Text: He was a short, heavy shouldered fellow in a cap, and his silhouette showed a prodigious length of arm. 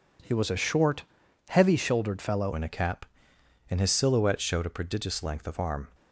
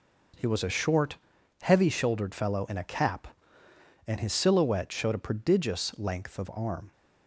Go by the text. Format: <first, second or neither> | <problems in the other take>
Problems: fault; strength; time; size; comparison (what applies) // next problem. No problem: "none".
second | changes voice at "in"; from 2.5 s on; 3.3 s long